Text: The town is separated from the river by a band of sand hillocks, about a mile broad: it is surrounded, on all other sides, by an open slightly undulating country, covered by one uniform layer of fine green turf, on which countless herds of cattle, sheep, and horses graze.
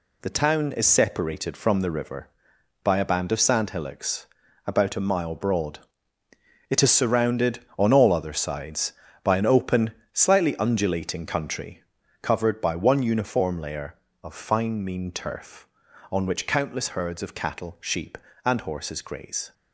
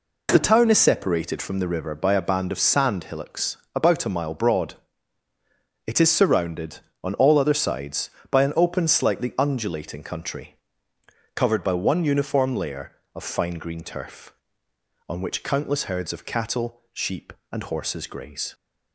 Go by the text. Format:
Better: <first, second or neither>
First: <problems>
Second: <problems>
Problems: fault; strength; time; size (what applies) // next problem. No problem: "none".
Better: second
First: pauses between "open" and "slightly"; slight; at 9.9 s; 0.20 s long // says "mean" for "green"; at 14.8 s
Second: none